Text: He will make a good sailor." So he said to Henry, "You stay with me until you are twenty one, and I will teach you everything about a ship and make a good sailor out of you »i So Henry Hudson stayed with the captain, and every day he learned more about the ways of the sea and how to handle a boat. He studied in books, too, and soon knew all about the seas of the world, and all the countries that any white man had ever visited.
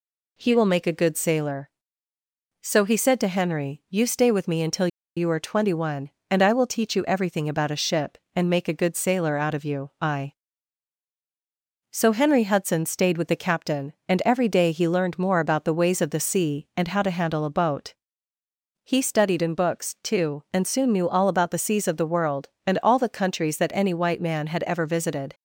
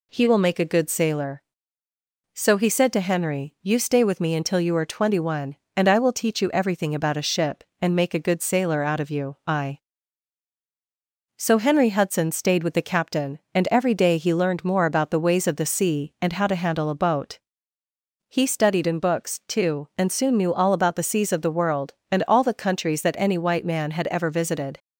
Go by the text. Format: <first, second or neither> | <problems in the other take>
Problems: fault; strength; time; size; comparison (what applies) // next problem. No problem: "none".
second | pauses between "until" and "you"; slight; at 4.8 s; 0.29 s long